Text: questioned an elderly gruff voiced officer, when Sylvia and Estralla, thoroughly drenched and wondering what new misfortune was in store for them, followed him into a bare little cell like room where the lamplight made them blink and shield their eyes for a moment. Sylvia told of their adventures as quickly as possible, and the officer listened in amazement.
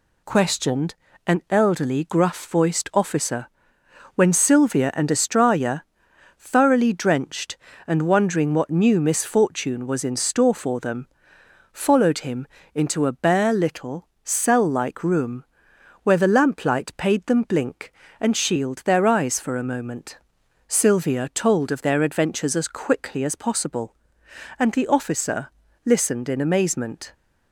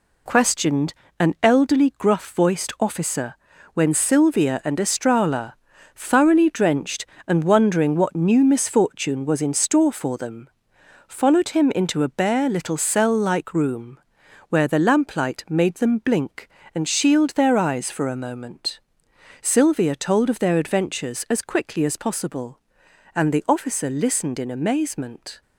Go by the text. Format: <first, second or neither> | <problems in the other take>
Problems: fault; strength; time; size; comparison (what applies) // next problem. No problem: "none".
second | pauses between "questioned" and "an"; slight; at 0.9 s; 0.32 s long; slight in the second // pauses between "him" and "into"; slight; at 12.4 s; 0.28 s long // pauses between "little" and "cell"; slight; at 14.0 s; 0.18 s long // pauses between "room" and "where"; noticeable; at 15.4 s; 0.58 s long; noticeable in the second // says "paid" for "made"; at 16.9 s // pauses between "officer" and "listened"; slight; at 25.5 s; 0.34 s long